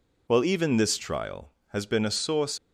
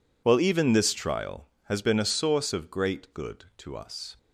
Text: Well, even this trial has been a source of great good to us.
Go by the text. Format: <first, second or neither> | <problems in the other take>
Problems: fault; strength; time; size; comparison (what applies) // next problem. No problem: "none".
second | stops before "of great good to us"; at 2.5 s